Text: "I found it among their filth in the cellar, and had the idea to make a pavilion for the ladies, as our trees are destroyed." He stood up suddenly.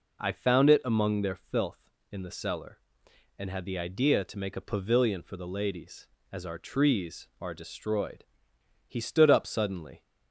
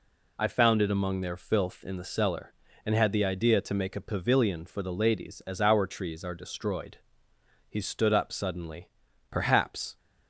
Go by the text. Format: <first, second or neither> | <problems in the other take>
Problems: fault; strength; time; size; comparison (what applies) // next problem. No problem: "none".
first | goes on to say "Perhaps"; noticeable; from 9.3 s on; 0.66 s long